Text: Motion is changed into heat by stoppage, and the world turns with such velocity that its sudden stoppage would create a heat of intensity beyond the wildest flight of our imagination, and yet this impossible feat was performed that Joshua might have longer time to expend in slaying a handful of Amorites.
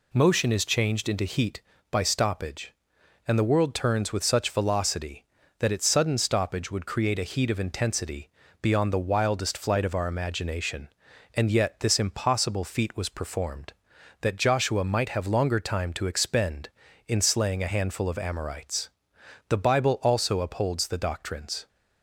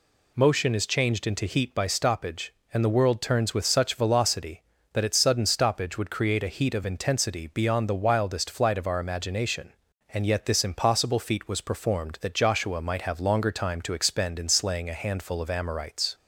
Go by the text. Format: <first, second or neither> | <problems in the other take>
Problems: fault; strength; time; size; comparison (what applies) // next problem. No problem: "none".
second | pauses between "intensity" and "beyond"; slight; at 8.2 s; 0.32 s long // goes on to say "The bible also upholds the doctrines"; strong; from 19.4 s on; 2.1 s long